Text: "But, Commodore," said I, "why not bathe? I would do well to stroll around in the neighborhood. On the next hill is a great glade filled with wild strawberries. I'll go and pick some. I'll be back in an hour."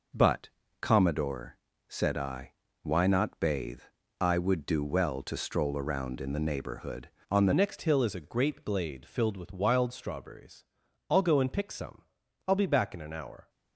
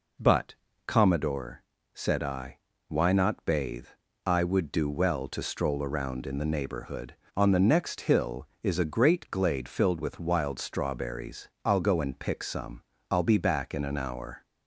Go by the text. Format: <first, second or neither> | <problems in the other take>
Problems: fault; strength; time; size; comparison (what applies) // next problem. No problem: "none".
second | changes voice at "next"; from 7.5 s on; 5.9 s long